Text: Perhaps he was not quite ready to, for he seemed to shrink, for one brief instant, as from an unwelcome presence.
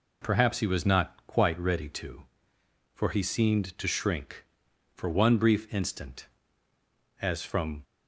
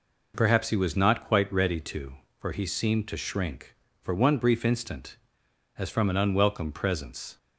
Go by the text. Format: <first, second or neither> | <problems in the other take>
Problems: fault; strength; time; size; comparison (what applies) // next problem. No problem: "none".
second | stops before "an unwelcome presence"; at 7.8 s